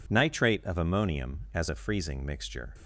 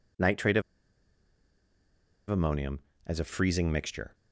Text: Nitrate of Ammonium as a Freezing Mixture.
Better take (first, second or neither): first